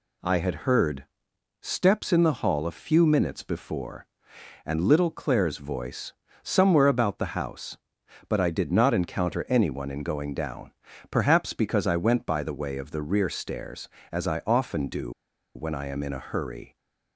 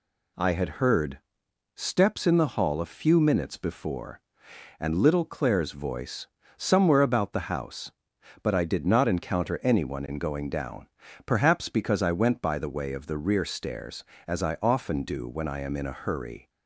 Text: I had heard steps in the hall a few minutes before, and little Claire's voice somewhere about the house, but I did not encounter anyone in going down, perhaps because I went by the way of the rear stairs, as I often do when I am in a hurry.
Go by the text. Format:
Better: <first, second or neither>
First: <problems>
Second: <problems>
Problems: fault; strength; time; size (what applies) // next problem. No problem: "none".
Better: second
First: pauses between "heard" and "steps"; noticeable; at 1.0 s; 0.58 s long // pauses between "voice" and "somewhere"; slight; at 6.1 s; 0.30 s long // pauses between "do" and "when"; at 15.1 s; 0.45 s long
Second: pauses between "heard" and "steps"; noticeable; at 1.1 s; 0.58 s long // pauses between "voice" and "somewhere"; slight; at 6.2 s; 0.30 s long